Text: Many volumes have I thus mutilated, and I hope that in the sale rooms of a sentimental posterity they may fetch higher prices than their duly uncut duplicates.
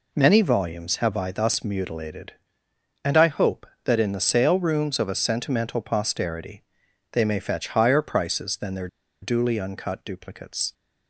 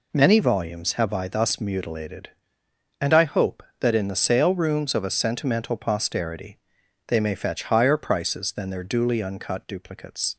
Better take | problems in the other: second | pauses between "posterity" and "they"; noticeable; at 6.6 s; 0.50 s long; noticeable in the second // pauses between "their" and "duly"; slight; at 8.8 s; 0.33 s long

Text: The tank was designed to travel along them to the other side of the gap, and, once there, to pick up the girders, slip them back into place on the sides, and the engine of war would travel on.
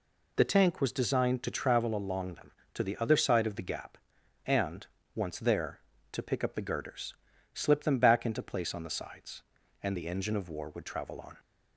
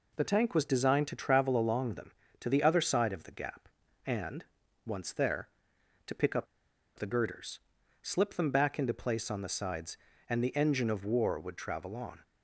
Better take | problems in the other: first | pauses between "up" and "the"; noticeable; at 6.4 s; 0.52 s long

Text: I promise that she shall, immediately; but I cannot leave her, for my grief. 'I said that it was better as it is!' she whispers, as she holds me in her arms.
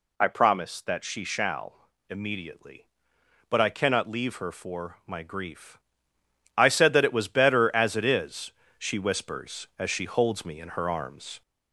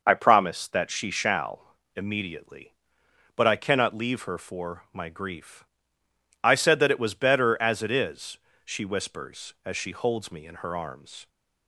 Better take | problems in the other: second | gets louder; slight; throughout; 3 dB

